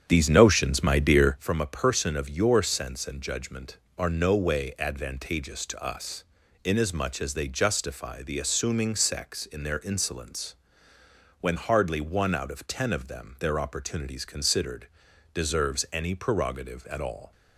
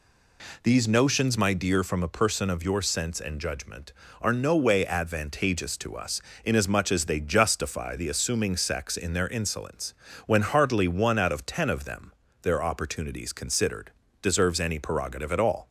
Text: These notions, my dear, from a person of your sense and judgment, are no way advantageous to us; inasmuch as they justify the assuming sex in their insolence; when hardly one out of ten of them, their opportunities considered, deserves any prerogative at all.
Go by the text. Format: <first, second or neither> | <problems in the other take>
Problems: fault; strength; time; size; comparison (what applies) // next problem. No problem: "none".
second | starts louder than the rest; strong; until 1.4 s; 8.5 dB